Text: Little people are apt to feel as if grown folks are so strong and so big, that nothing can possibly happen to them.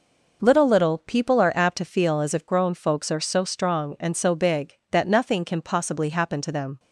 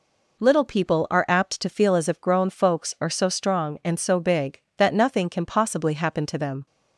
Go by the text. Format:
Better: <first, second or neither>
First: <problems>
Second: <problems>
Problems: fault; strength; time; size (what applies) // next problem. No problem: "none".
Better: second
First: says "Little" twice; at 0.6 s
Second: none